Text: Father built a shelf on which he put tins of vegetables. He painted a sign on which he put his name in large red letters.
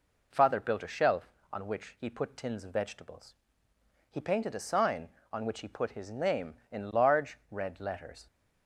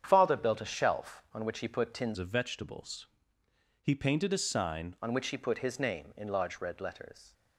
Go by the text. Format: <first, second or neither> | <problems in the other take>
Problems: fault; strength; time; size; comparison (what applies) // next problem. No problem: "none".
first | starts louder than the rest; strong; until 1.0 s; 8.5 dB // changes voice from "of" to "sign"; from 2.1 to 4.9 s; 2.8 s long